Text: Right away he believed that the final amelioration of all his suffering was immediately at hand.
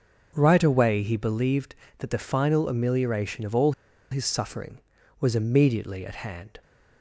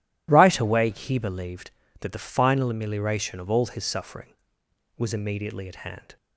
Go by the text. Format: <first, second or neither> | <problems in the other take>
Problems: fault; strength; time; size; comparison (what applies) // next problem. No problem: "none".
second | pauses between "all" and "his"; at 3.7 s; 0.39 s long